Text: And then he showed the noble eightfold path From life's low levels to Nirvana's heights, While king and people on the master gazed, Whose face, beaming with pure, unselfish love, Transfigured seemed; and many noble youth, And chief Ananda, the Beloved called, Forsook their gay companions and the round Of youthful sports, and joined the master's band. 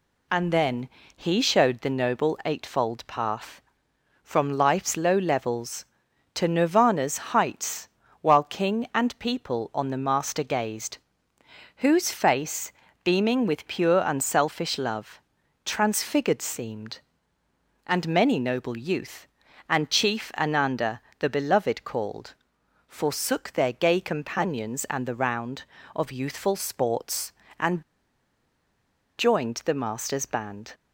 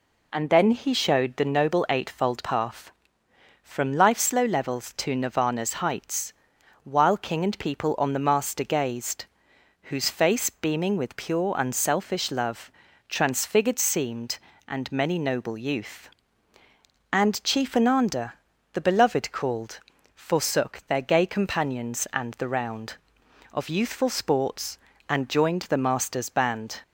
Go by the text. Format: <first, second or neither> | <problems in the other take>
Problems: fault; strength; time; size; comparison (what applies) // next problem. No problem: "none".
second | pauses between "then" and "he"; slight; at 0.8 s; 0.28 s long // pauses between "Nirvana's" and "heights"; slight; at 7.1 s; 0.16 s long // pauses between "and" and "joined"; strong; at 27.8 s; 1.3 s long